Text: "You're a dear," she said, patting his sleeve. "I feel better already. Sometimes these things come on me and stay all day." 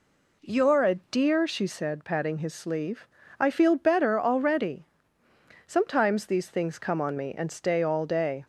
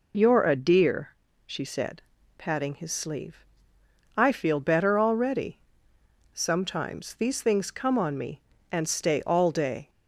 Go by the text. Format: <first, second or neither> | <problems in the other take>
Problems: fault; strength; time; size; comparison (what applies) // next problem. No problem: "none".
neither | none